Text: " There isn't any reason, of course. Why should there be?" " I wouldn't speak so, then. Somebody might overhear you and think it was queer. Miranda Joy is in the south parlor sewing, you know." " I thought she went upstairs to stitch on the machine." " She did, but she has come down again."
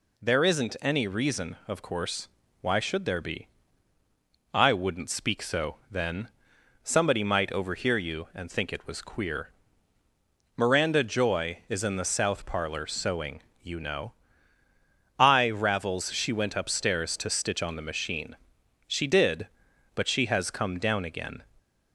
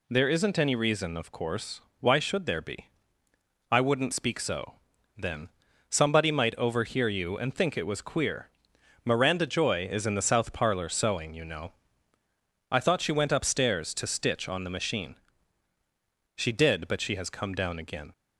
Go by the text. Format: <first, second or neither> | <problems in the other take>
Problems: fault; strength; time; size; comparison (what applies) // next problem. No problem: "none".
second | says "ravels" for "thought"; at 15.5 s